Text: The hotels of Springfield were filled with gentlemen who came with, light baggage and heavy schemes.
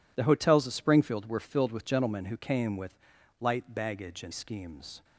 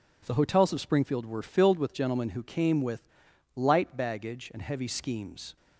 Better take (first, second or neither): second